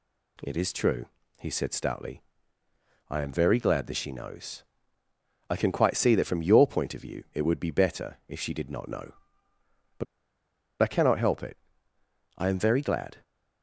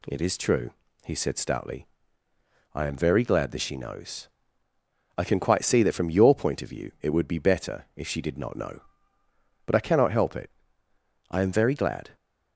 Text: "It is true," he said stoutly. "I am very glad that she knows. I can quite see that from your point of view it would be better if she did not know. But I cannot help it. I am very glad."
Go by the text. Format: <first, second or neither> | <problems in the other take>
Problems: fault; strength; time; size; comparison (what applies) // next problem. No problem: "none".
second | pauses between "But" and "I"; noticeable; at 10.0 s; 0.77 s long